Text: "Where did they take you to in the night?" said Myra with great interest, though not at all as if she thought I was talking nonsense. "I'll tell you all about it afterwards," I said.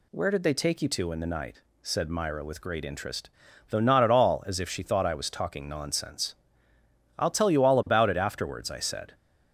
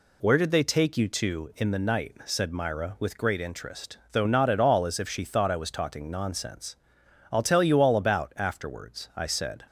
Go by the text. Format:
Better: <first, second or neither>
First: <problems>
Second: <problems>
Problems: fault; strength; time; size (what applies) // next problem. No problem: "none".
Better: first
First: none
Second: skips "it"; at 8.3 s